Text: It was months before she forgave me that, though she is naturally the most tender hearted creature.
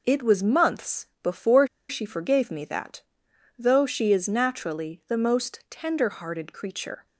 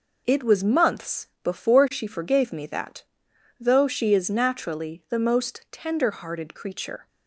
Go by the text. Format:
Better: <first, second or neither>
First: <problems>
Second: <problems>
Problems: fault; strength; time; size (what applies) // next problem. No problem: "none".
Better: second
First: pauses between "months" and "before"; slight; at 1.0 s; 0.16 s long // pauses between "before" and "she"; slight; at 1.6 s; 0.23 s long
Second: pauses between "months" and "before"; slight; at 1.2 s; 0.16 s long